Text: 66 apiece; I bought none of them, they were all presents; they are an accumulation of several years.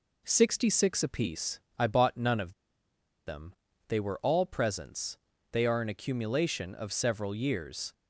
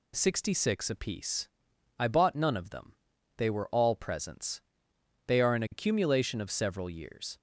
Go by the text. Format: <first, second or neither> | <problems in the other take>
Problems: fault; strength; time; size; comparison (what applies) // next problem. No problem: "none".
second | pauses between "of" and "them"; noticeable; at 2.5 s; 0.73 s long